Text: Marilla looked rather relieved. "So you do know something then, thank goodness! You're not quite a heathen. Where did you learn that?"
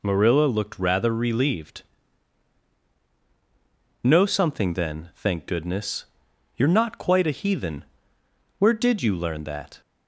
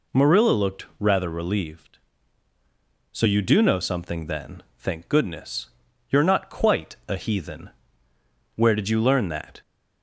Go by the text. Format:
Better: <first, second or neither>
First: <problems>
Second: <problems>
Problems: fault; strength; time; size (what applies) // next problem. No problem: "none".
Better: second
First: skips "So you do"; at 2.9 s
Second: none